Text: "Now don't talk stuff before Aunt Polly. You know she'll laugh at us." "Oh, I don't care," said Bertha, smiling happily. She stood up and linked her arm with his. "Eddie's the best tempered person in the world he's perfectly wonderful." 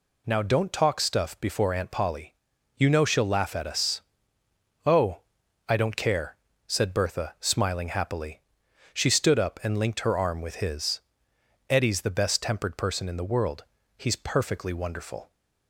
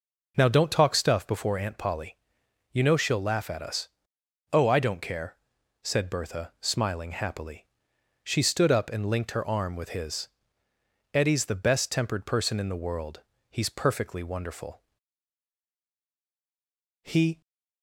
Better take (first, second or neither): first